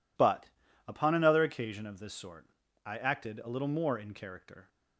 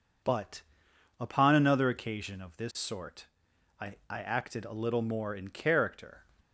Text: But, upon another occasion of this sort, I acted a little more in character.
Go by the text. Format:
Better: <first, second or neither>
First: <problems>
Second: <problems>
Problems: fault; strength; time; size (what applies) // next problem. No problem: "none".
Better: first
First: none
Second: says "I" twice; at 4.0 s